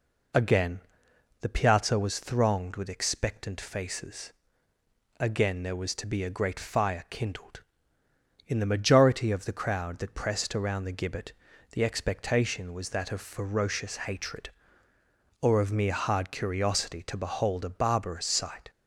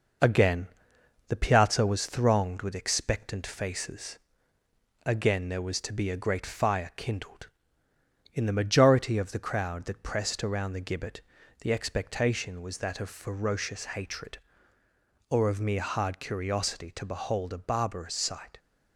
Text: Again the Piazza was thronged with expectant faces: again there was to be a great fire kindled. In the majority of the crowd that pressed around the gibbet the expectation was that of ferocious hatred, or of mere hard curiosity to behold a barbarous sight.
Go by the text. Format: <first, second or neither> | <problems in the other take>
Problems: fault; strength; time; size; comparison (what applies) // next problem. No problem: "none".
first | gets quieter; slight; throughout; 3.5 dB // pauses between "Again" and "the"; noticeable; at 0.6 s; 0.60 s long; noticeable in the first // pauses between "gibbet" and "the"; at 11.1 s; 0.42 s long; also in the first